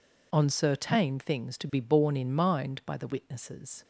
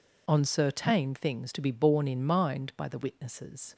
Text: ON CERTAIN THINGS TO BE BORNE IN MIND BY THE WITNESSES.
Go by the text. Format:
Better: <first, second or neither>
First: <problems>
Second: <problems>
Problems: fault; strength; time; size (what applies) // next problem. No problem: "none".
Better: neither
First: none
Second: none